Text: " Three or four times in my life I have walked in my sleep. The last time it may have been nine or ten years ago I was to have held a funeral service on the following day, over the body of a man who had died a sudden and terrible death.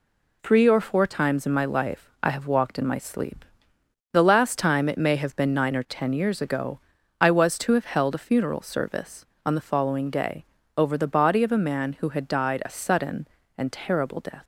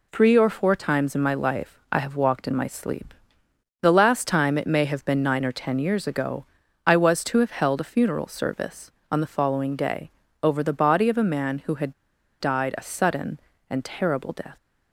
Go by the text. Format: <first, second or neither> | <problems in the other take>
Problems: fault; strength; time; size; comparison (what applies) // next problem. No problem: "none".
first | pauses between "ago" and "I"; at 6.4 s; 0.38 s long; also in the first // pauses between "had" and "died"; noticeable; at 11.9 s; 0.46 s long